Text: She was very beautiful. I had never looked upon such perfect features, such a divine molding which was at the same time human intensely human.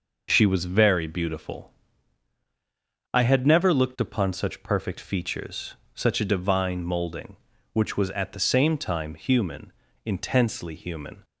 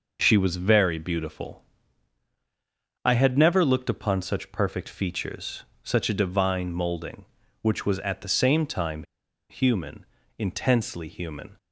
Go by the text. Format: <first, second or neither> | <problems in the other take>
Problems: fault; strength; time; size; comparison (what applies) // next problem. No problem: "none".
first | pauses between "time" and "human"; noticeable; at 9.0 s; 0.47 s long // pauses between "human" and "intensely"; slight; at 10.0 s; 0.32 s long; slight in the first